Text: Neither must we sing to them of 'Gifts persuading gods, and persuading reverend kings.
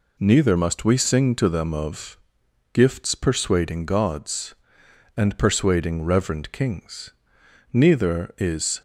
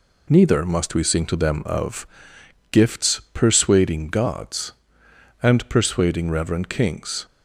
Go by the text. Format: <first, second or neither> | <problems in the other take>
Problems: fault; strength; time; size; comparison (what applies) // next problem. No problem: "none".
second | pauses between "of" and "Gifts"; noticeable; at 2.1 s; 0.56 s long; noticeable in the second // goes on to say "Neither is"; noticeable; from 7.7 s on; 1.1 s long